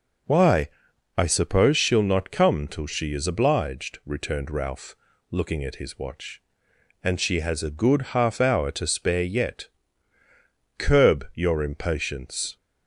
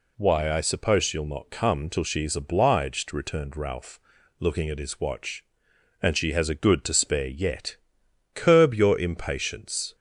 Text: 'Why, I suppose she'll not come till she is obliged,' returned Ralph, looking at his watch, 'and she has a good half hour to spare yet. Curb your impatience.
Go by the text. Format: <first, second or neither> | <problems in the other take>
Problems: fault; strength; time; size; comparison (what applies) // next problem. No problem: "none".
first | skips "half hour"; at 6.8 s